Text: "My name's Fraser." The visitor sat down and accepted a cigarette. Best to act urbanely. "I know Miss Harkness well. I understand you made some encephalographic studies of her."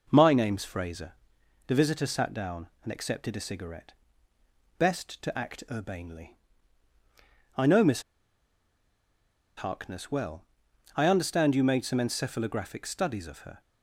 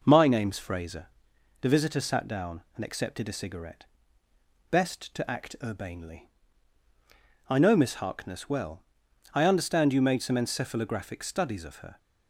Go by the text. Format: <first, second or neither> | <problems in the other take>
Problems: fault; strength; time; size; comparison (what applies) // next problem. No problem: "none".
second | pauses between "Miss" and "Harkness"; strong; at 8.0 s; 1.5 s long